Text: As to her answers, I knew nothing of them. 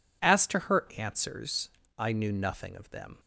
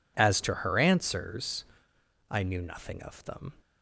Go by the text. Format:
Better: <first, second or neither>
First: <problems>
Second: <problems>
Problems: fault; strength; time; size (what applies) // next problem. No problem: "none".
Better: neither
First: none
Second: none